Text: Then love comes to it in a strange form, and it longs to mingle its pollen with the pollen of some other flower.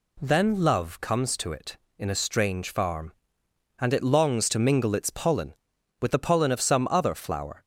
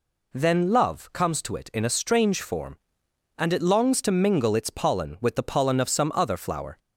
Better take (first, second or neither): second